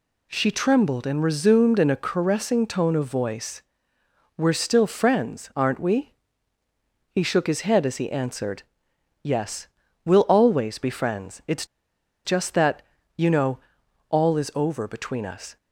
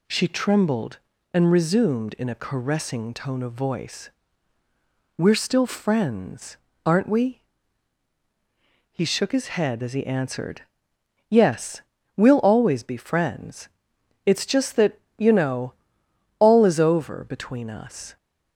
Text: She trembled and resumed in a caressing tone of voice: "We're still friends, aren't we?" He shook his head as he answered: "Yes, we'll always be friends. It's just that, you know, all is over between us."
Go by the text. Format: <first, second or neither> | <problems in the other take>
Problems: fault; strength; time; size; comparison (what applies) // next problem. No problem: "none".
second | pauses between "It's" and "just"; noticeable; at 11.6 s; 0.60 s long